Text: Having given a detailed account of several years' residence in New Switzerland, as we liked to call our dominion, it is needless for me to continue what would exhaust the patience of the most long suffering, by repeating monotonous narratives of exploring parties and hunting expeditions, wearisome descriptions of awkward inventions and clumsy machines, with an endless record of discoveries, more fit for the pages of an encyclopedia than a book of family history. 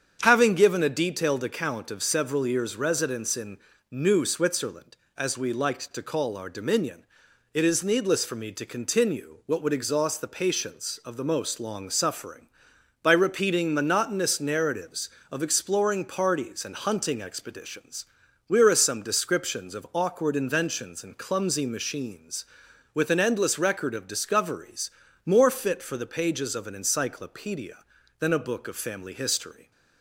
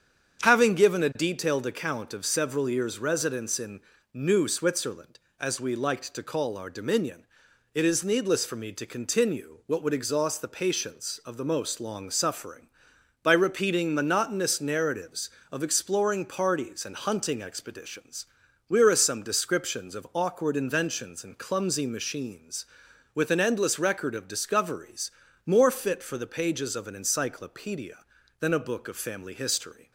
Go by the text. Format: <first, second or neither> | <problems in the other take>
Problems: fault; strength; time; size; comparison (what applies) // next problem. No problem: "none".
neither | starts louder than the rest; strong; the same in both // pauses between "in" and "New"; slight; the same in both